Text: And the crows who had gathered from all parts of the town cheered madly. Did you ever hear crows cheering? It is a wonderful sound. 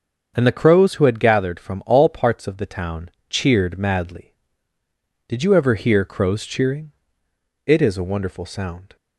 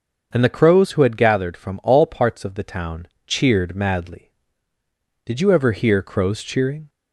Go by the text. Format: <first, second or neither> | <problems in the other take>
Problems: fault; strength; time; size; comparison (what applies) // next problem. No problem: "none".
first | starts louder than the rest; until 1.3 s; 6.5 dB; also in the first // pauses between "town" and "cheered"; slight; at 3.0 s; 0.20 s long; slight in the first // stops before "It is a wonderful sound"; at 6.8 s